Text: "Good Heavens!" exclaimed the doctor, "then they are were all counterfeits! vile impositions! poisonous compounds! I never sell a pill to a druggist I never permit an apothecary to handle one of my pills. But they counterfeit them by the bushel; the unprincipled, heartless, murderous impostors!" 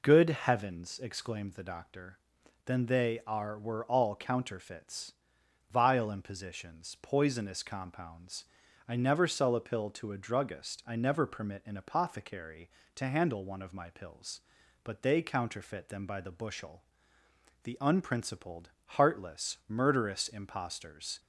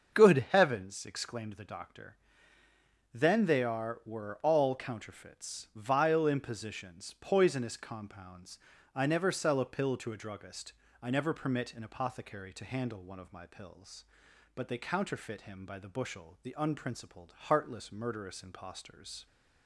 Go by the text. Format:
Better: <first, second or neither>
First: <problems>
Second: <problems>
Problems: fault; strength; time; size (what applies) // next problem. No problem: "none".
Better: first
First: none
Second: starts louder than the rest; until 1.2 s; 6.5 dB // pauses between "druggist" and "I"; slight; at 10.7 s; 0.30 s long // says "him" for "them"; at 15.4 s